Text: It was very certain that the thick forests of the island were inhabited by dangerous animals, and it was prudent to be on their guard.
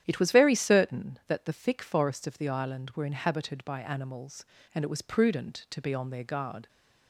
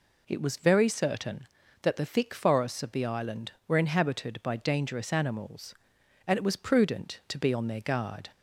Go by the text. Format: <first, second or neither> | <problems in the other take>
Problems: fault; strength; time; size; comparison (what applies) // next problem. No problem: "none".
second | starts louder than the rest; strong; until 1.0 s; 10.5 dB // skips "dangerous"; at 3.7 s